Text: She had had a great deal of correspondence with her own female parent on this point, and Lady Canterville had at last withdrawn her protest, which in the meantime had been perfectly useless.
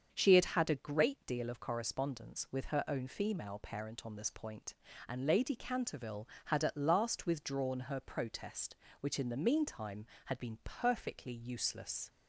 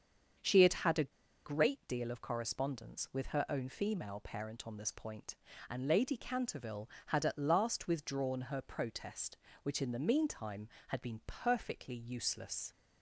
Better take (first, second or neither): first